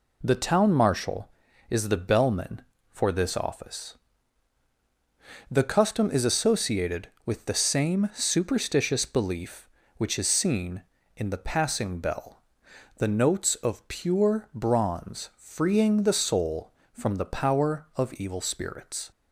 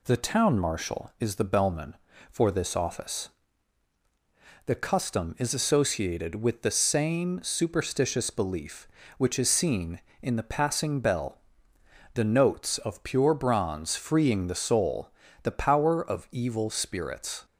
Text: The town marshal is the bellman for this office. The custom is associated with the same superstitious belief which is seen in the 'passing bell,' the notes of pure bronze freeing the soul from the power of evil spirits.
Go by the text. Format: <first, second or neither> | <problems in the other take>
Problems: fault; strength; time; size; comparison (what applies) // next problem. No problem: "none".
first | skips "from"; at 15.2 s